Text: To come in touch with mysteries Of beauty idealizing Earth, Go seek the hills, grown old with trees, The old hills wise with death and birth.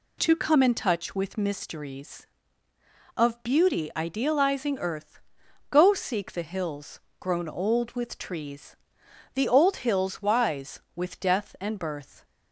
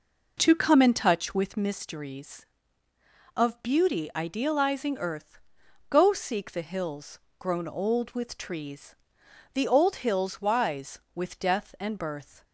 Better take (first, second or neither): first